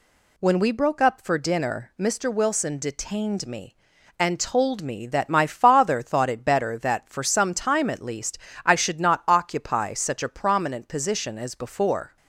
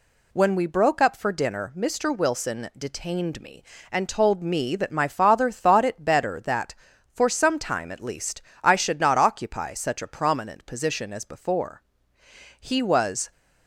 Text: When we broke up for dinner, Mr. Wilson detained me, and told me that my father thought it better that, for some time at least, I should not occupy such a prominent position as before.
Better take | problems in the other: first | goes on to say "He was"; noticeable; from 12.6 s on; 0.70 s long

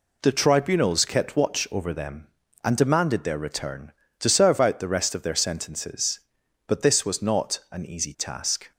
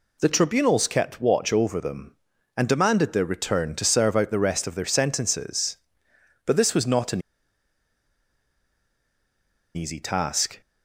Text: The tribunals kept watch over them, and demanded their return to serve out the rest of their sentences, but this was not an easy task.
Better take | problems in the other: first | pauses between "an" and "easy"; strong; at 7.2 s; 2.5 s long

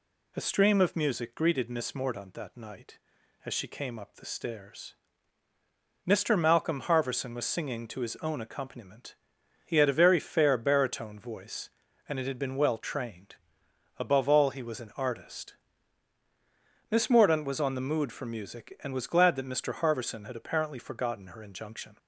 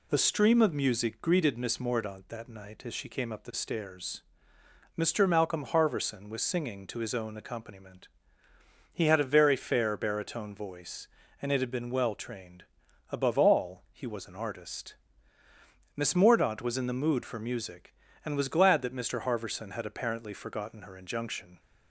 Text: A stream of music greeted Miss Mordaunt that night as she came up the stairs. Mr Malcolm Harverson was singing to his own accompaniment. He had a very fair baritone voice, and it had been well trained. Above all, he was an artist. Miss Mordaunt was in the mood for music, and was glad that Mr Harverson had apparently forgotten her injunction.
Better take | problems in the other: second | says "on" for "in"; at 17.6 s

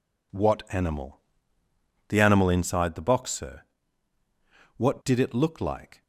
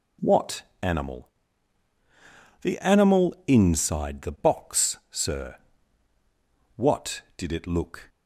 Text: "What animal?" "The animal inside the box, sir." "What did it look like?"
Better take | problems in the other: first | pauses between "What" and "animal"; slight; at 0.6 s; 0.18 s long // stops before "like"; at 8.0 s

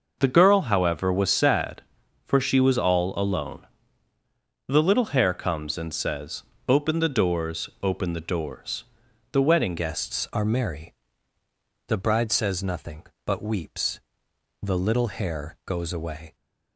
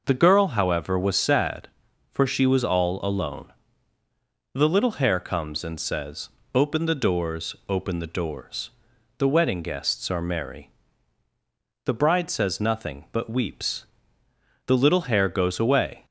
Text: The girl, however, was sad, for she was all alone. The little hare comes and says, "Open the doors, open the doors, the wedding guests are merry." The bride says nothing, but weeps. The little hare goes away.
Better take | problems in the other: second | changes voice at "guests"; from 9.7 s on; 6.6 s long

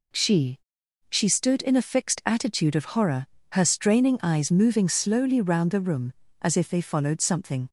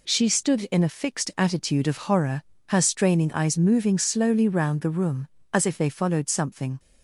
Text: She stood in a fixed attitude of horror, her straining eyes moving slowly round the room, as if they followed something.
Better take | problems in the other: second | says "She" twice; at 1.1 s

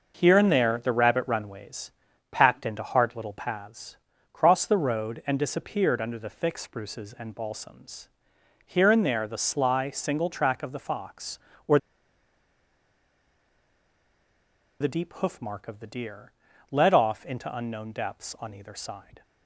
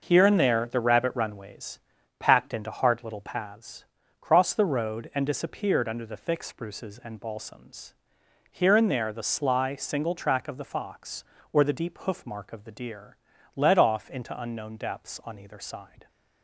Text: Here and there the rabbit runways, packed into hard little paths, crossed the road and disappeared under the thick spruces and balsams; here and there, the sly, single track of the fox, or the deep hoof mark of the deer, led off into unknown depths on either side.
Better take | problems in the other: second | pauses between "or" and "the"; strong; at 11.7 s; 3.0 s long

